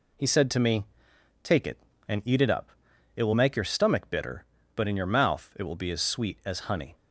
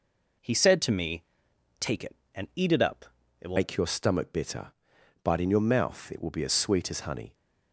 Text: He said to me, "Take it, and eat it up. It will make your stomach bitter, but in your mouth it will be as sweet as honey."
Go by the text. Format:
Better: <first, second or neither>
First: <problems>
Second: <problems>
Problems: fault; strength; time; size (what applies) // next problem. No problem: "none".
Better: first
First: none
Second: changes voice at "make"; from 3.5 s on; 3.8 s long